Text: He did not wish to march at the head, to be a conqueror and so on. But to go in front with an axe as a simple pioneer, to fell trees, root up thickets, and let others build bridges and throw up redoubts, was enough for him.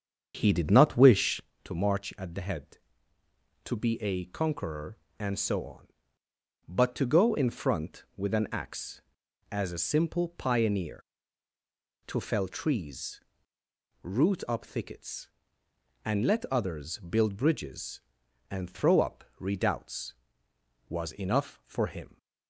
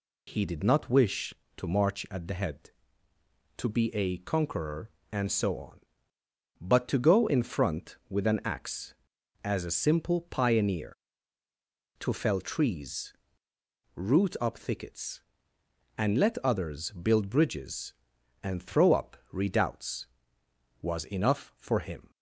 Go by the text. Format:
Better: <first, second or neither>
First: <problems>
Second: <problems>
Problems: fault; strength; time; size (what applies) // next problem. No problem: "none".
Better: second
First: starts louder than the rest; strong; until 1.5 s; 7.5 dB // pauses between "up" and "redoubts"; slight; at 19.2 s; 0.16 s long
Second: pauses between "up" and "redoubts"; slight; at 19.1 s; 0.16 s long